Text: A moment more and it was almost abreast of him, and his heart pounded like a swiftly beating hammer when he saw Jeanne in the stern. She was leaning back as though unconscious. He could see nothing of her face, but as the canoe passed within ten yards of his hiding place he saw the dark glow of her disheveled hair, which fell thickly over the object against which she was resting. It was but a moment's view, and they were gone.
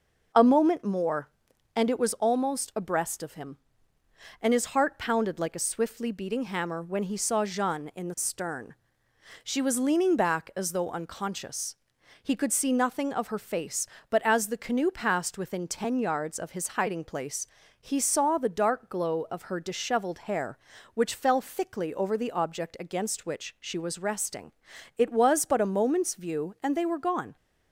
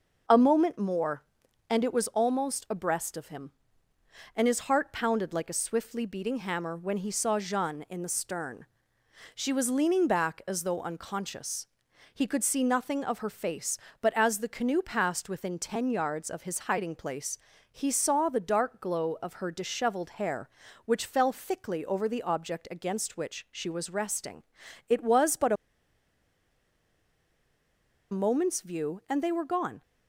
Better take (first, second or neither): first